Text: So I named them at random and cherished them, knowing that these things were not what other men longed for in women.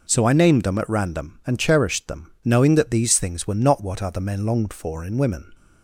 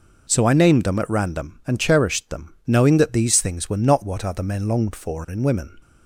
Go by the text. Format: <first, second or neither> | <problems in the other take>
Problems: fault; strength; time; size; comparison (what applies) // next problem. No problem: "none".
neither | none